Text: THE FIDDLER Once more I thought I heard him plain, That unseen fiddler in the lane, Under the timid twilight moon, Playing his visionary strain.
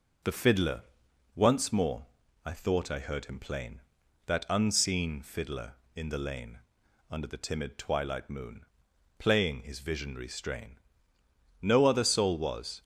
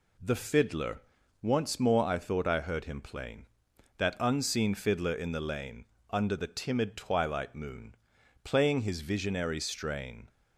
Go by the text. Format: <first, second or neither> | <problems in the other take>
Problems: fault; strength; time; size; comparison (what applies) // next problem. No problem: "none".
second | pauses between "FIDDLER" and "Once"; noticeable; at 0.8 s; 0.50 s long; also in the second // pauses between "more" and "I"; at 2.0 s; 0.38 s long // goes on to say "No other soul was"; noticeable; from 11.6 s on; 1.2 s long